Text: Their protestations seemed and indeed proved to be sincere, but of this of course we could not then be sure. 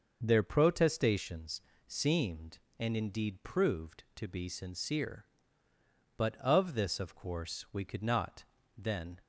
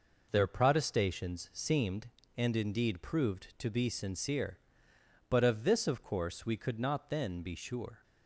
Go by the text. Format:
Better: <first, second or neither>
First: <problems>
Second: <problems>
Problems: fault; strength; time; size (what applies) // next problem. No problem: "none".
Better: second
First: starts louder than the rest; noticeable; until 1.2 s; 6 dB // pauses between "protestations" and "seemed"; slight; at 1.6 s; 0.26 s long // pauses between "not" and "then"; slight; at 8.4 s; 0.34 s long // stops before "be sure"; at 9.2 s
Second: none